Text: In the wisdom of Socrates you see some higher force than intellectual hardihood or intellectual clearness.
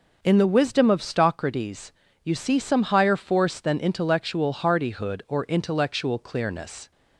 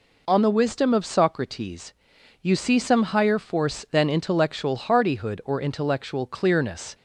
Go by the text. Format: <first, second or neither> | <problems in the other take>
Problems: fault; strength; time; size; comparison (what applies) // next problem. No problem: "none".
first | says "On" for "In"; at 0.2 s // pauses between "Socrates" and "you"; noticeable; at 1.9 s; 0.50 s long; slight in the first